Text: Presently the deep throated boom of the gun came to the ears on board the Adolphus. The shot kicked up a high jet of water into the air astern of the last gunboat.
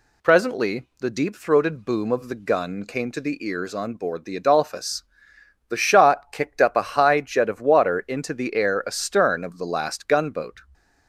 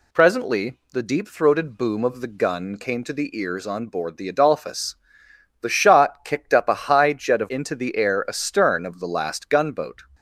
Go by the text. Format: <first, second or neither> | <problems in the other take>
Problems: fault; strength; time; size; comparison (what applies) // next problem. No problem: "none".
first | skips "water"; at 7.4 s